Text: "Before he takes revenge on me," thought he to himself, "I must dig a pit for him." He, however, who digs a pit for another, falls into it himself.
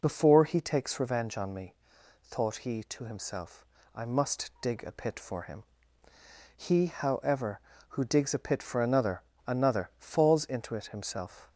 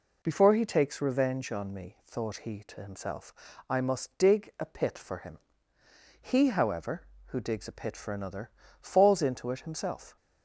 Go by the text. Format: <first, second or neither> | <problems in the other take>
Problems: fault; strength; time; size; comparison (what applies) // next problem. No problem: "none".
second | says "another" twice; at 9.4 s